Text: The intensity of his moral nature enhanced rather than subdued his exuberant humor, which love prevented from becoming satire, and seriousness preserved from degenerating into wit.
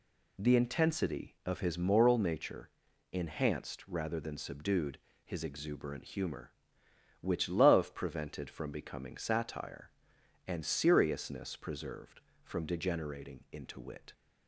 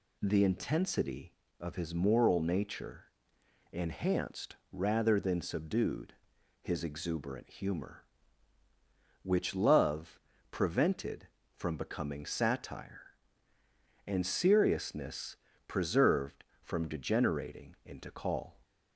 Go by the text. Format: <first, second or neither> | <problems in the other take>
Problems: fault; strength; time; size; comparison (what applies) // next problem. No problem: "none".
first | pauses between "nature" and "enhanced"; noticeable; at 3.0 s; 0.66 s long; also in the first // pauses between "enhanced" and "rather"; slight; at 4.5 s; 0.16 s long // pauses between "subdued" and "his"; noticeable; at 6.1 s; 0.48 s long; slight in the first // pauses between "love" and "prevented"; slight; at 10.1 s; 0.32 s long // pauses between "seriousness" and "preserved"; slight; at 15.3 s; 0.32 s long // says "call" for "wit"; at 18.1 s